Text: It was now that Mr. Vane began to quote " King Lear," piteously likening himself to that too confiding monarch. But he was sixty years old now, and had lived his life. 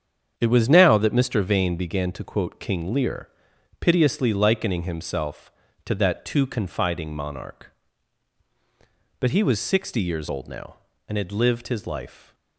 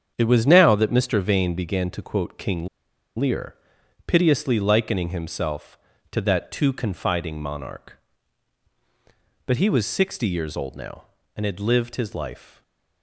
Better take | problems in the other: first | starts louder than the rest; strong; until 1.1 s; 7.5 dB; strong in the first // pauses between "King" and "Lear"; noticeable; at 2.6 s; 0.49 s long // stays silent after the last word; slight; from 12.5 s on; 0.5 s long

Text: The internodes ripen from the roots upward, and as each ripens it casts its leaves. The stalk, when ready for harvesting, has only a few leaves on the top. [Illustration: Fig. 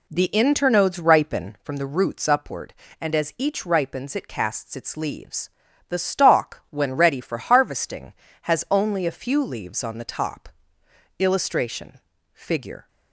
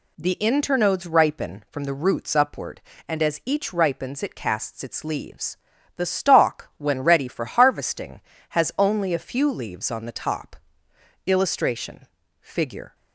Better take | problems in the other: second | starts louder than the rest; slight; until 1.7 s; 3 dB

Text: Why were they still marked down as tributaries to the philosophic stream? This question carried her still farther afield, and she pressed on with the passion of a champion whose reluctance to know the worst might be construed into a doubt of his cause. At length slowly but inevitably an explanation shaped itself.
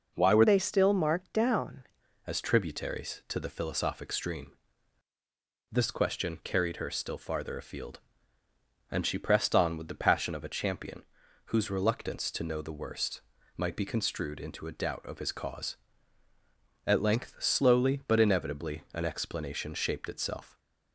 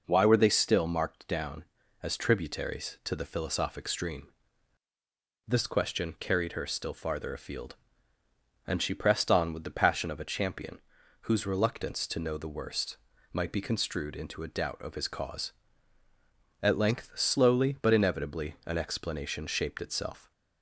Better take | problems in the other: second | changes voice from "they" to "down"; from 0.4 to 1.8 s; 1.4 s long // pauses between "champion" and "whose"; at 11.0 s; 0.44 s long; also in the second // pauses between "worst" and "might"; slight; at 13.2 s; 0.34 s long; slight in the second

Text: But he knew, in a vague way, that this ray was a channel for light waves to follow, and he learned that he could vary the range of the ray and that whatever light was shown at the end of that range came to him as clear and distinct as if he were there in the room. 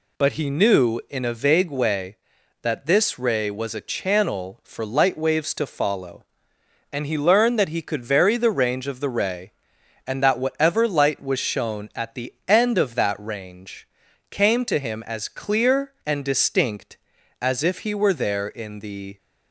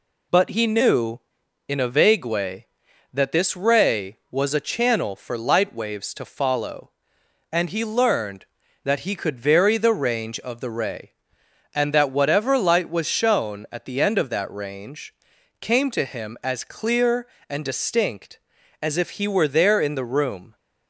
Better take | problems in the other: second | pauses between "range" and "came"; at 13.8 s; 0.44 s long; noticeable in the second // stops before "room"; at 19.1 s

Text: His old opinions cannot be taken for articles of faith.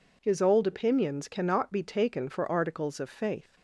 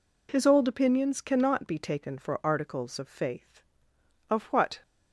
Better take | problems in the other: first | goes on to say "Of what"; from 4.2 s on; 0.54 s long

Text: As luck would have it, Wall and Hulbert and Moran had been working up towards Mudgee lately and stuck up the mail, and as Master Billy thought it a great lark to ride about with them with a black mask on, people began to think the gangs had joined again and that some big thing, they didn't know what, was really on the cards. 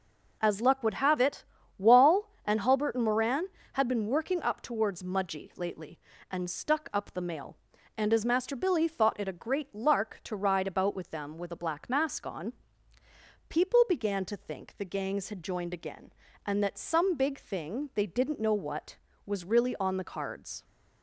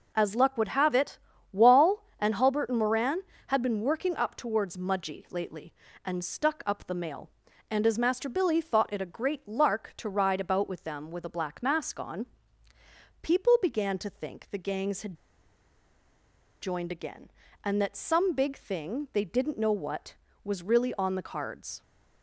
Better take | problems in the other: first | pauses between "had" and "joined"; strong; at 15.1 s; 1.4 s long

